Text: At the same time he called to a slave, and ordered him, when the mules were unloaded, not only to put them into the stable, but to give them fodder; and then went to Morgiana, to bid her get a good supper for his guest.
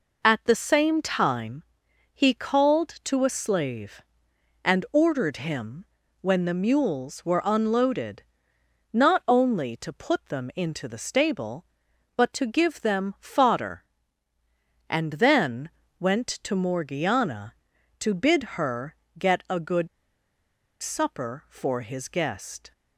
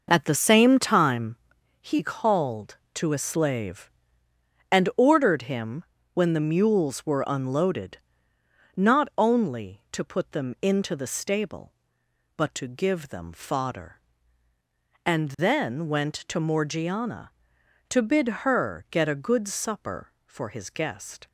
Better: second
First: pauses between "time" and "he"; noticeable; at 1.6 s; 0.50 s long // pauses between "then" and "went"; slight; at 15.7 s; 0.28 s long // pauses between "her" and "get"; slight; at 18.9 s; 0.24 s long // pauses between "good" and "supper"; noticeable; at 19.8 s; 0.93 s long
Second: pauses between "time" and "he"; noticeable; at 1.3 s; 0.46 s long

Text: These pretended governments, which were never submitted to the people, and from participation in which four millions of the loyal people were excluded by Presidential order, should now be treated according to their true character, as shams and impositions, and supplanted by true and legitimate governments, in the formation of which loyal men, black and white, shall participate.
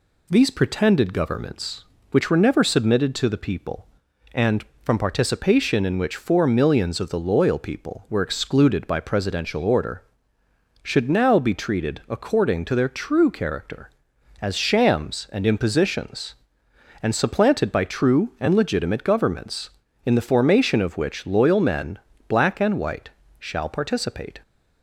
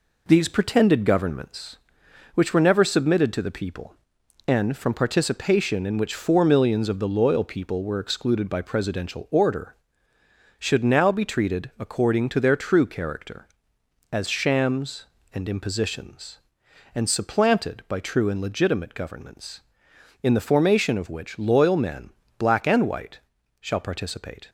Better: first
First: none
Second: gets quieter; noticeable; throughout; 4.5 dB

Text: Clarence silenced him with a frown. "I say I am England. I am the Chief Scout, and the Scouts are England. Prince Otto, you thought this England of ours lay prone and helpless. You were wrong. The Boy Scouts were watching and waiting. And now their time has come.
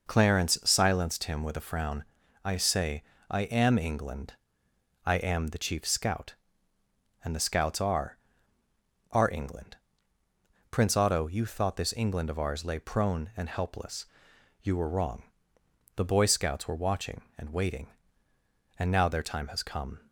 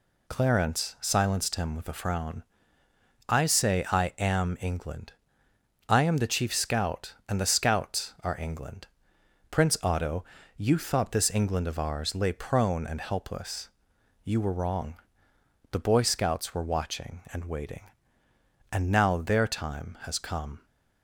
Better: second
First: pauses between "say" and "I"; slight; at 3.0 s; 0.26 s long // says "are" twice; at 9.1 s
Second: none

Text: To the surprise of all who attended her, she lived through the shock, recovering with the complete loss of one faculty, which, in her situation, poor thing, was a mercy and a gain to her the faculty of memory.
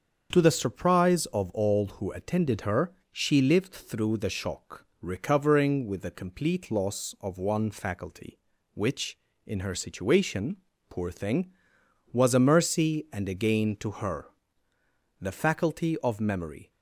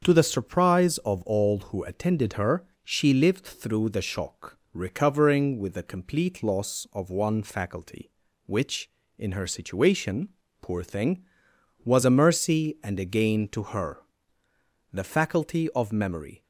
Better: neither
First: starts louder than the rest; until 1.3 s; 6.5 dB // pauses between "her" and "the"; noticeable; at 14.2 s; 0.94 s long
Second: starts louder than the rest; until 1.0 s; 6.5 dB // pauses between "her" and "the"; noticeable; at 13.9 s; 0.94 s long

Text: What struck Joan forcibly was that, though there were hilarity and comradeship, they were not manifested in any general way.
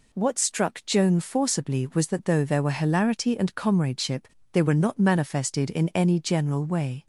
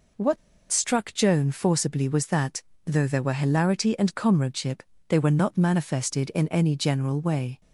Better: first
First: none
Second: pauses between "What" and "struck"; slight; at 0.3 s; 0.33 s long

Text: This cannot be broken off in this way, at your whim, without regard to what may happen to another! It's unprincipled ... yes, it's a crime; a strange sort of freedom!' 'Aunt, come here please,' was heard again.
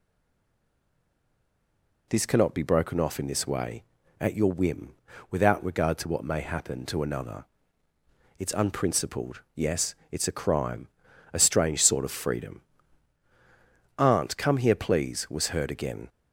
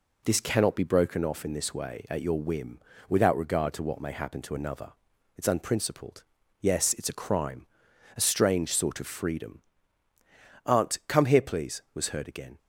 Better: second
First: stays silent before the first word; noticeable; until 2.0 s; 2.0 s long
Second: none

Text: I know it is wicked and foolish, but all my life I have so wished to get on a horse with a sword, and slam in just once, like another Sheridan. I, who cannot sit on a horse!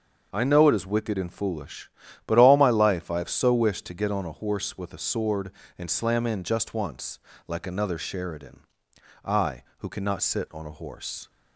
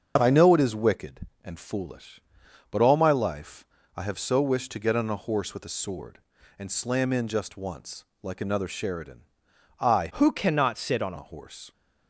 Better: first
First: starts louder than the rest; until 1.3 s; 6.5 dB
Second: starts louder than the rest; until 1.2 s; 6.5 dB // pauses between "life" and "I"; slight; at 3.6 s; 0.30 s long // changes voice from "who" to "on"; from 10.1 to 11.1 s; 1.0 s long

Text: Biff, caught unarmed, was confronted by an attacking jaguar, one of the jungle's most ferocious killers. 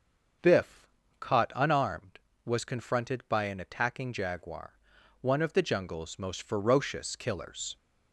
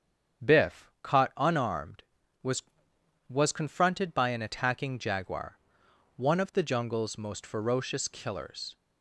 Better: first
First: starts louder than the rest; until 1.7 s; 6.5 dB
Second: starts louder than the rest; strong; until 1.5 s; 7.5 dB // says "was" twice; at 3.2 s

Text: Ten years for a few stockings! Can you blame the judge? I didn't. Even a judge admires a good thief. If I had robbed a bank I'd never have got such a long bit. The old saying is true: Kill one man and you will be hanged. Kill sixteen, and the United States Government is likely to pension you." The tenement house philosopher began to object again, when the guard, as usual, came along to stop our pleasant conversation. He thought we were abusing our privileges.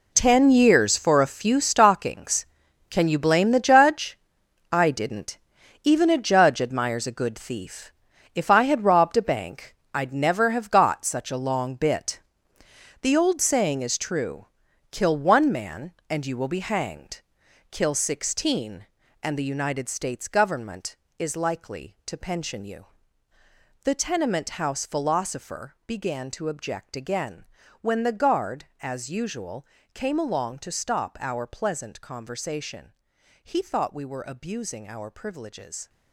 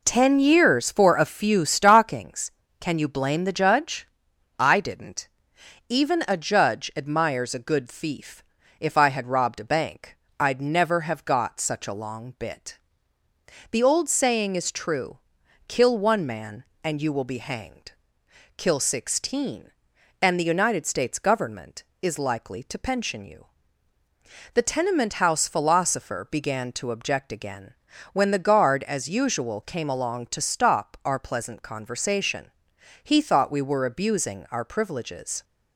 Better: second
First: gets quieter; strong; throughout; 12.5 dB // pauses between "bank" and "I'd"; slight; at 9.7 s; 0.18 s long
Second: pauses between "bank" and "I'd"; slight; at 10.1 s; 0.22 s long

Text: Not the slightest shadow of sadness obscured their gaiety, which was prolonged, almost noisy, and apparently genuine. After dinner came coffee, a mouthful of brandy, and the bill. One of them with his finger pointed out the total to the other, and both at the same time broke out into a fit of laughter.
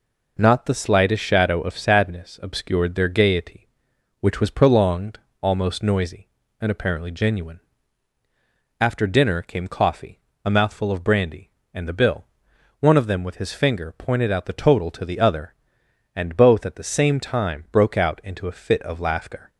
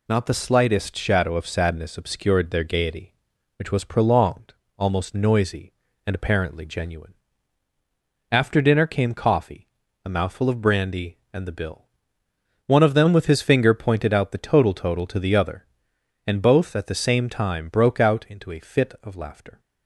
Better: first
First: none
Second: says "total" twice; at 14.7 s

